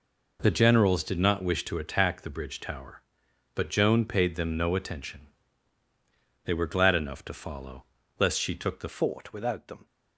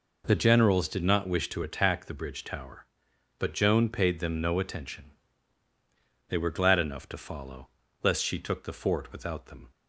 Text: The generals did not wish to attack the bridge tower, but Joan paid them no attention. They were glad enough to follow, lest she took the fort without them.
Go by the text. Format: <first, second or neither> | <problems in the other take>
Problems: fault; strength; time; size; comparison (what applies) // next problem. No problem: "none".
second | changes voice at "fort"; from 8.8 s on; 1.0 s long